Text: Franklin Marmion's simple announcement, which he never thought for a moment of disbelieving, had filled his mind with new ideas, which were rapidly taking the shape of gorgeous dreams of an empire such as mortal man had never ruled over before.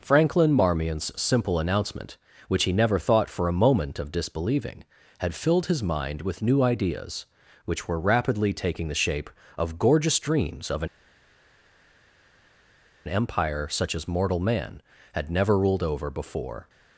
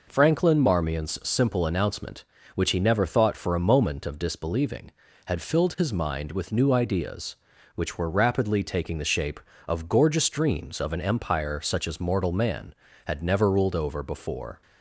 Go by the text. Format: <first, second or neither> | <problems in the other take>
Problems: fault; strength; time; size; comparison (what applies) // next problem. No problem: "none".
second | pauses between "an" and "empire"; strong; at 10.8 s; 2.1 s long